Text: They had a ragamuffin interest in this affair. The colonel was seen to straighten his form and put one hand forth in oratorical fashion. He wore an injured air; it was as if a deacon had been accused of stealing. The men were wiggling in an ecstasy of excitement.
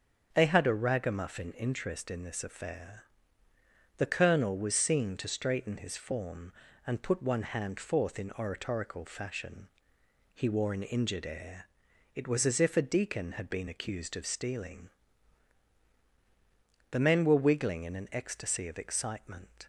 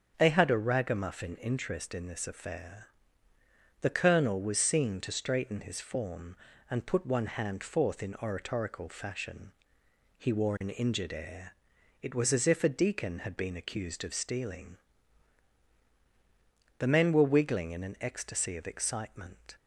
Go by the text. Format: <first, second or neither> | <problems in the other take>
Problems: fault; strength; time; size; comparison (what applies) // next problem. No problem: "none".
neither | starts louder than the rest; the same in both